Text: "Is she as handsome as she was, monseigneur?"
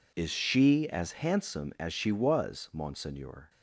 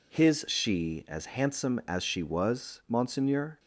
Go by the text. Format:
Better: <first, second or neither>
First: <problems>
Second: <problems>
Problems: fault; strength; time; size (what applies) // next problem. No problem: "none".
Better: first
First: none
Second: says "His" for "Is"; at 0.1 s